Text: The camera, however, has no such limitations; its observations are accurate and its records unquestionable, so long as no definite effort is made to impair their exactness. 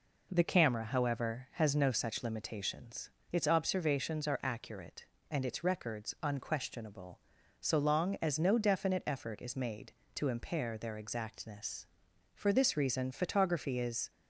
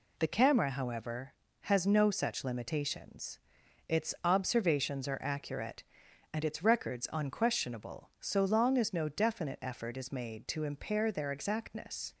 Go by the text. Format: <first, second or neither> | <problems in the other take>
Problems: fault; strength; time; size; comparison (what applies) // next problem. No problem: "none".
second | goes on to say "For this reason photography is"; strong; from 12.3 s on; 1.7 s long